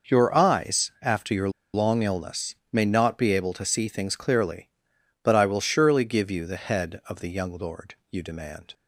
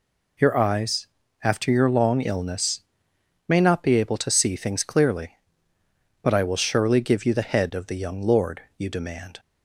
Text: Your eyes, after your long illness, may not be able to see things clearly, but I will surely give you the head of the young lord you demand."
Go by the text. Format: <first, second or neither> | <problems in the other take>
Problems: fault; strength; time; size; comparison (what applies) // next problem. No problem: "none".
second | pauses between "your" and "long"; slight; at 1.4 s; 0.24 s long // pauses between "lord" and "you"; slight; at 7.9 s; 0.16 s long; slight in the second